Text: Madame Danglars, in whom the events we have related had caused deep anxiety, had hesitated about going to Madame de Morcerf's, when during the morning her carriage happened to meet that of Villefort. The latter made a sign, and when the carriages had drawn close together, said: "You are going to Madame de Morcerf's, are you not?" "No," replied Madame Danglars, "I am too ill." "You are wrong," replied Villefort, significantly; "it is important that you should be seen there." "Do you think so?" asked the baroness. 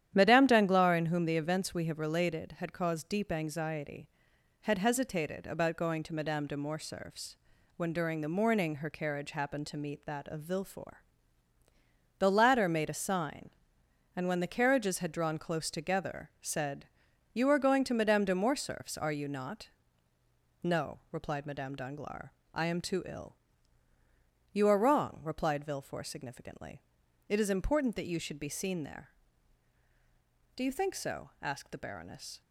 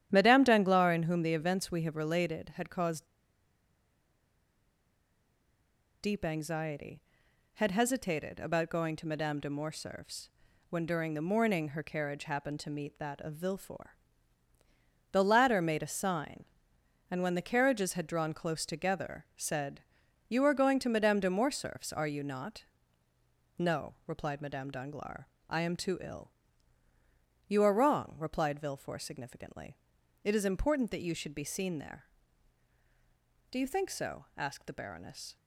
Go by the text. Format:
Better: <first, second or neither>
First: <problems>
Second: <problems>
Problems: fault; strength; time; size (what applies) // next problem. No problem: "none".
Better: first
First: starts louder than the rest; strong; until 1.1 s; 10.5 dB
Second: starts louder than the rest; strong; until 1.1 s; 10.5 dB // pauses between "caused" and "deep"; strong; at 3.0 s; 2.9 s long